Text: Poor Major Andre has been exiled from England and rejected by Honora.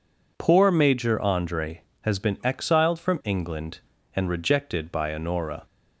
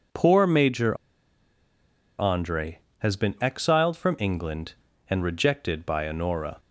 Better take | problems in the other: first | pauses between "Major" and "Andre"; at 0.9 s; 1.2 s long

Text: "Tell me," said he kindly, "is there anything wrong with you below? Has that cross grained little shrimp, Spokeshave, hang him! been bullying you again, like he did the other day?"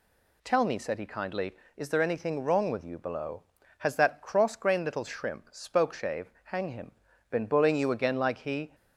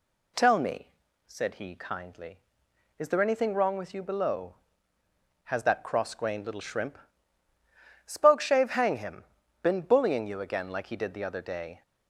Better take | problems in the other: second | stops before "did the other day"; at 8.7 s

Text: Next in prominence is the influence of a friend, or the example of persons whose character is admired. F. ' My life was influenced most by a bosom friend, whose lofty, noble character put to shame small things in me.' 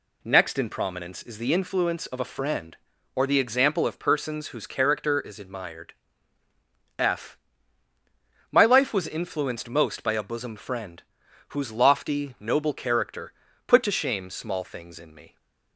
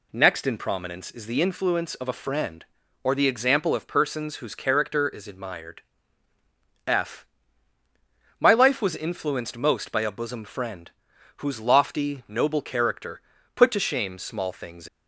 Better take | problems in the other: first | pauses between "character" and "put"; slight; at 13.2 s; 0.34 s long; slight in the first // stops before "in me"; at 14.8 s

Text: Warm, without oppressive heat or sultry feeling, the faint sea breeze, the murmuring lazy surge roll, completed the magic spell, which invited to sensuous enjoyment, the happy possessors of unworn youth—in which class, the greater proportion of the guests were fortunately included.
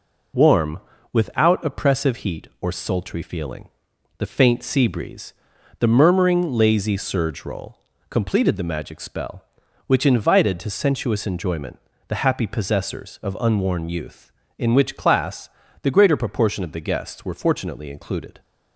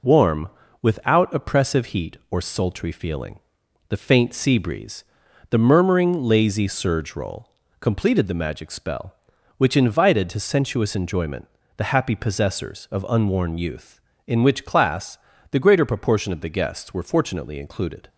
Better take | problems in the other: neither | none

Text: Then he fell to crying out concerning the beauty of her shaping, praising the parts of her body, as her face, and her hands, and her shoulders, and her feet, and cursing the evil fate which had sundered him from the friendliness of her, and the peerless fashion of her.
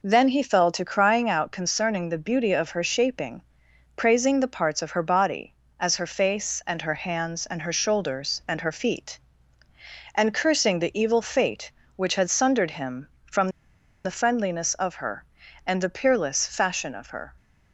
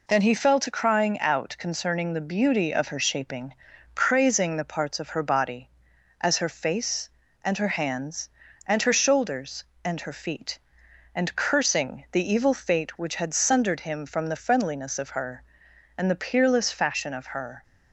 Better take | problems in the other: second | pauses between "from" and "the"; noticeable; at 13.4 s; 0.55 s long

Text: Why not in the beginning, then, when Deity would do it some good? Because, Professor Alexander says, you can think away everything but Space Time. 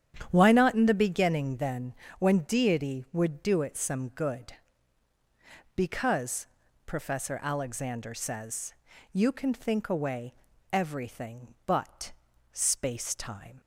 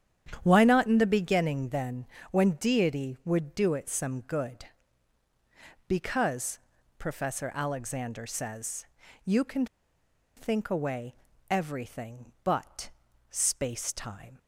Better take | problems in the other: first | starts louder than the rest; strong; until 1.4 s; 9.5 dB; strong in the first // pauses between "can" and "think"; noticeable; at 9.6 s; 0.71 s long // pauses between "away" and "everything"; slight; at 11.1 s; 0.36 s long; also in the first // pauses between "but" and "Space"; at 12.8 s; 0.40 s long; also in the first

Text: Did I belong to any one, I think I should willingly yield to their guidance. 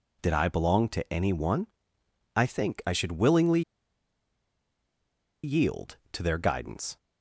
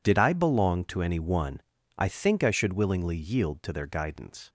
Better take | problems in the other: second | pauses between "willingly" and "yield"; strong; at 3.6 s; 1.8 s long

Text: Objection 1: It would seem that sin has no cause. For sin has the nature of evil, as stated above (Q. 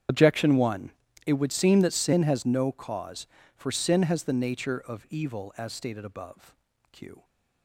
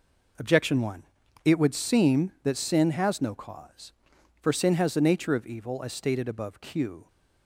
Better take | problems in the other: second | loses the start of "Objection"; at 0.0 s; 35 ms // starts louder than the rest; strong; until 1.4 s; 8.5 dB

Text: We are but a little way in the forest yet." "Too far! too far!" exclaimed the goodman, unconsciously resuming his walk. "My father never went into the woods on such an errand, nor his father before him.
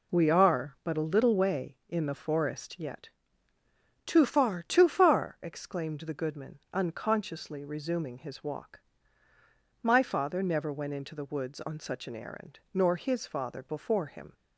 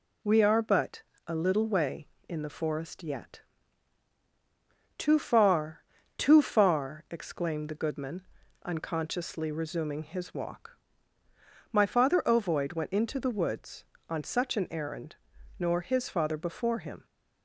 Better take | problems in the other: first | pauses between "but" and "a"; slight; at 1.0 s; 0.26 s long // says "ovoid" for "never"; at 12.2 s

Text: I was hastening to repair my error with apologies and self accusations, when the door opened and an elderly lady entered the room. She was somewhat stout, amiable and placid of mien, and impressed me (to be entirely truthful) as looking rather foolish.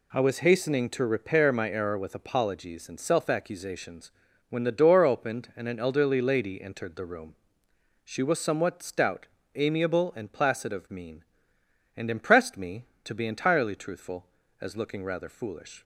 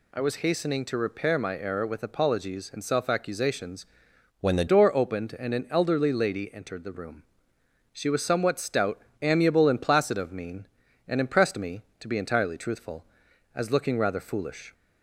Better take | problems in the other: first | changes voice from "when" to "the"; from 4.4 to 4.6 s; 0.2 s long

